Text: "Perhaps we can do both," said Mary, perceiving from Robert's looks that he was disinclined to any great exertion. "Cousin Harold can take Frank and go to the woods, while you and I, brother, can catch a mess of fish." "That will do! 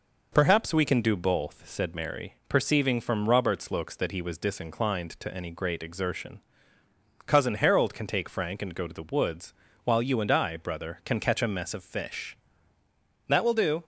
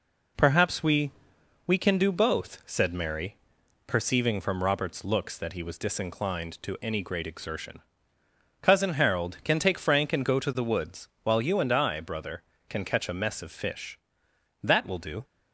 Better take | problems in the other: first | says "we" twice; at 1.6 s

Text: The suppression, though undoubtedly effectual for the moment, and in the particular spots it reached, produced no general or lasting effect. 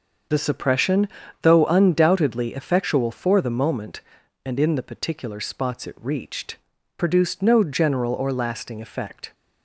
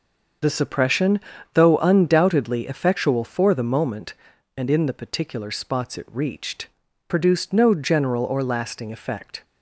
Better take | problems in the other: neither | starts louder than the rest; the same in both

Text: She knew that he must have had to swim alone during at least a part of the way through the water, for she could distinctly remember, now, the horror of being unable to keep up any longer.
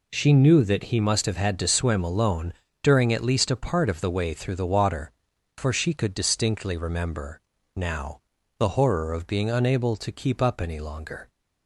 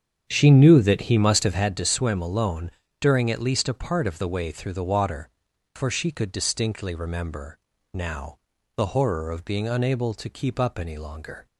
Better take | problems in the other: first | starts louder than the rest; strong; until 1.8 s; 8 dB // pauses between "alone" and "during"; slight; at 2.7 s; 0.28 s long; slight in the first

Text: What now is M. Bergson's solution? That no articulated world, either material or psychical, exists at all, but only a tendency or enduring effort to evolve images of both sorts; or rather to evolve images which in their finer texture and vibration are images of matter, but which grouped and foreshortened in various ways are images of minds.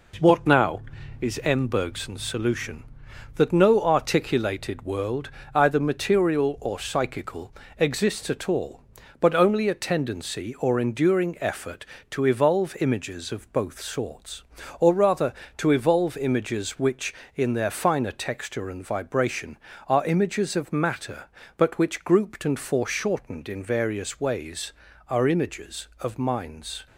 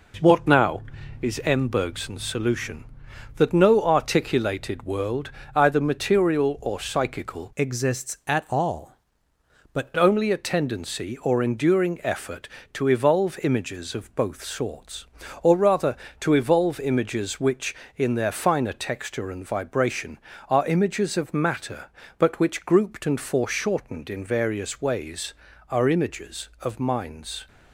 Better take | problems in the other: first | changes voice from "exists" to "but"; from 7.5 to 9.9 s; 2.4 s long

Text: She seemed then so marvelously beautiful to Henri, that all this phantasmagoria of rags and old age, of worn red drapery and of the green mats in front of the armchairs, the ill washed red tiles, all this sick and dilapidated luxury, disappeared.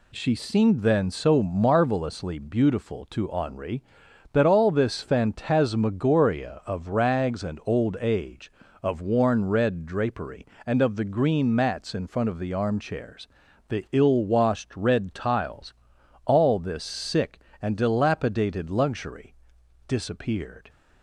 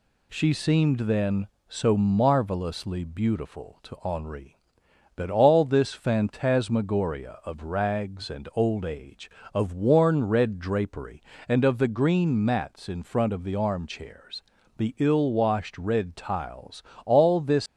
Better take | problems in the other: first | stops before "sick and dilapidated luxury disappeared"; at 17.6 s

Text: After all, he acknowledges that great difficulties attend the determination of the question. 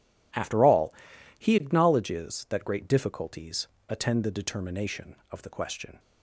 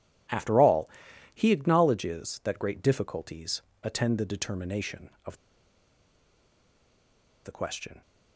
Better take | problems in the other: first | pauses between "difficulties" and "attend"; slight; at 3.6 s; 0.22 s long; slight in the first // pauses between "of" and "the"; strong; at 5.3 s; 2.0 s long

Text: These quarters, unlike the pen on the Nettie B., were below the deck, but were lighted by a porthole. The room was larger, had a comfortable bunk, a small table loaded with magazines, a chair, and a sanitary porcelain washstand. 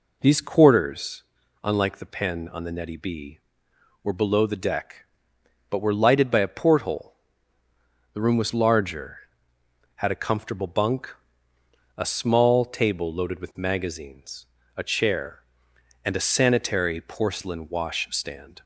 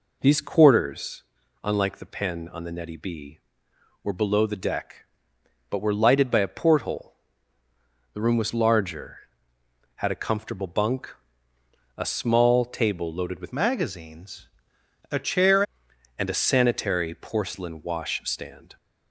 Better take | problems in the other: first | changes voice from "magazines" to "chair"; from 13.5 to 15.6 s; 2.1 s long

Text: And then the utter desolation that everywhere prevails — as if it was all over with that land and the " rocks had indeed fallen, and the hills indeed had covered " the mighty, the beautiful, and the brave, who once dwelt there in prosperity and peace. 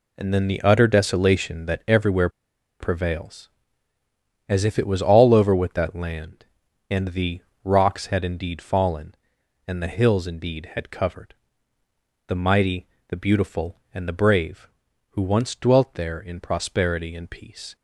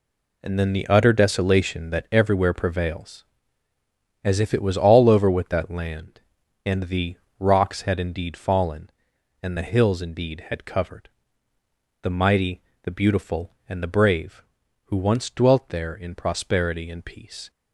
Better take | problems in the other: second | pauses between "everywhere" and "prevails"; noticeable; at 2.2 s; 0.51 s long

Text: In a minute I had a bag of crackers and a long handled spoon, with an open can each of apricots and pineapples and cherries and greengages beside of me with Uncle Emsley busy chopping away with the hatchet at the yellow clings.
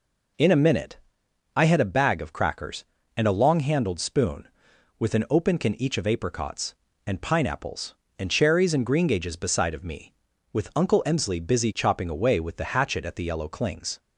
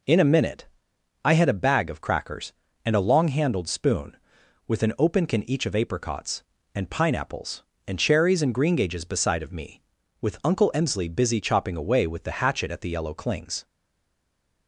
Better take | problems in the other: first | pauses between "minute" and "I"; noticeable; at 0.6 s; 0.56 s long; noticeable in the first // stays silent after the last word; from 13.6 s on; 1.0 s long

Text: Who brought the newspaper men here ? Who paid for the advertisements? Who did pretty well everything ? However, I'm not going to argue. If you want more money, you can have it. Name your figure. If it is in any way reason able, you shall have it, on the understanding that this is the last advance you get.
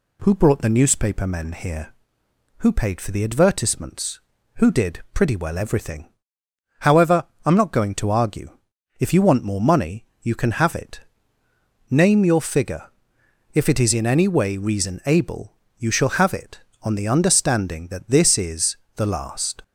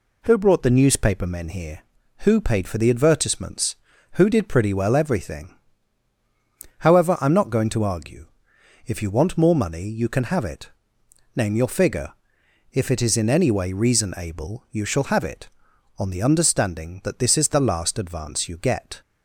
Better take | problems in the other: second | pauses between "is" and "the"; slight; at 18.7 s; 0.20 s long // stops before "advance you get"; at 19.6 s

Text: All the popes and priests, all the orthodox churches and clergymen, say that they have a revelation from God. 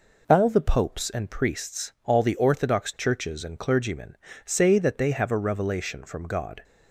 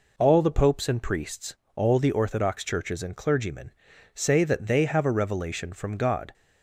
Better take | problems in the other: neither | none

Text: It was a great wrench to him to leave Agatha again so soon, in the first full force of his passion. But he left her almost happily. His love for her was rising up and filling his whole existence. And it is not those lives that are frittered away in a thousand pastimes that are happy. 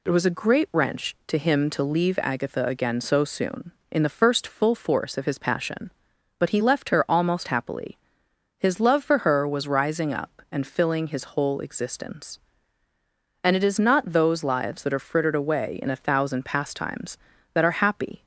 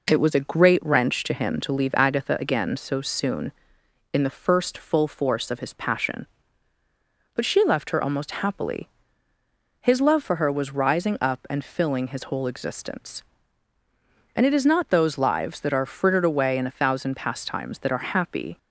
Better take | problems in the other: first | says "she" for "he"; at 7.4 s

